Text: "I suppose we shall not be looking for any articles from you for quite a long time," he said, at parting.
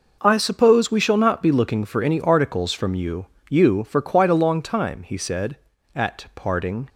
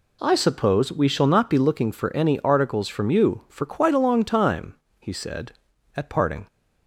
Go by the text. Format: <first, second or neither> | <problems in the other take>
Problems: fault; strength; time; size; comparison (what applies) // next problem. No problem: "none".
second | says "you" twice; at 3.4 s